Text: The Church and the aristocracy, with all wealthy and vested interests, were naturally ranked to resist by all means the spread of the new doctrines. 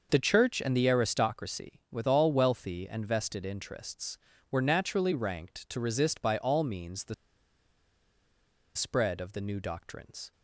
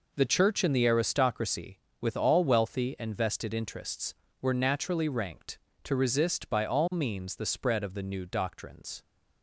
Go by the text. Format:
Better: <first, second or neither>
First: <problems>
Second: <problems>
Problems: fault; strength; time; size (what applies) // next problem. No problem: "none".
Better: second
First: starts louder than the rest; until 1.1 s; 6 dB // pauses between "the" and "spread"; strong; at 7.1 s; 1.6 s long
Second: none